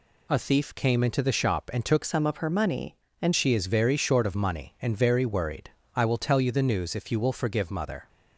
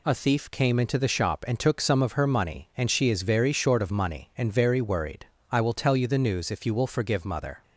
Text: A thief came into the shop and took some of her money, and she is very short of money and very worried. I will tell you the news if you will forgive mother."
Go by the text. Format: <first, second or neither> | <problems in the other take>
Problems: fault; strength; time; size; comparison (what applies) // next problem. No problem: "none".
second | changes voice from "some" to "and"; from 2.0 to 3.3 s; 1.3 s long